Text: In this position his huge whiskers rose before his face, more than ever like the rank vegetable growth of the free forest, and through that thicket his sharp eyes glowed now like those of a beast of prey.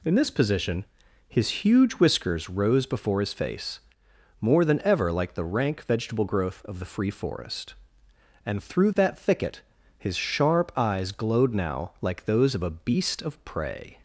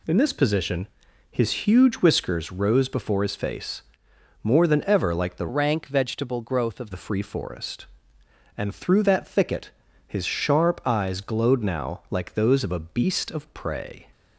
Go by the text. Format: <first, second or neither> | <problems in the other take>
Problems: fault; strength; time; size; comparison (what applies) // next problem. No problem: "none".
first | pauses between "position" and "his"; at 0.8 s; 0.44 s long; also in the first // changes voice from "rank" to "of"; from 5.4 to 6.8 s; 1.4 s long // pauses between "thicket" and "his"; slight; at 9.6 s; 0.36 s long; slight in the first